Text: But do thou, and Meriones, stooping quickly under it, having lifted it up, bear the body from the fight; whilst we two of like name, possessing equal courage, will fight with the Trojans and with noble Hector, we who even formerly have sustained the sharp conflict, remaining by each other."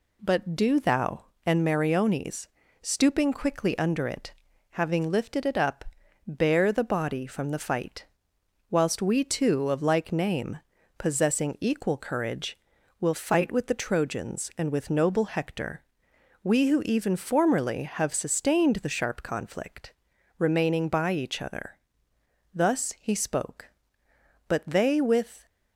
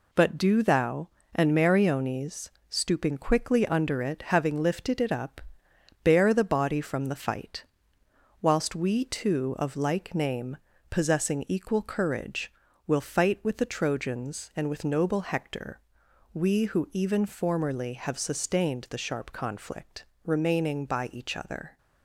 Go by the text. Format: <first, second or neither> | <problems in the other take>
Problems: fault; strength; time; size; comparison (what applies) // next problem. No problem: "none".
second | goes on to say "Thus he spoke but they with"; strong; from 22.5 s on; 2.9 s long